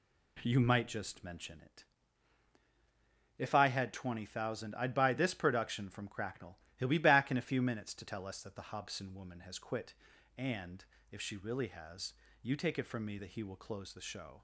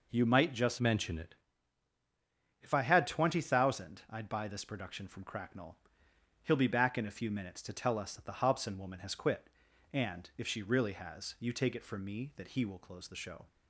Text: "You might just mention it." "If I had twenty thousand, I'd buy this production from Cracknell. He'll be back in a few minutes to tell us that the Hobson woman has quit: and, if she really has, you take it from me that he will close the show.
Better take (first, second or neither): first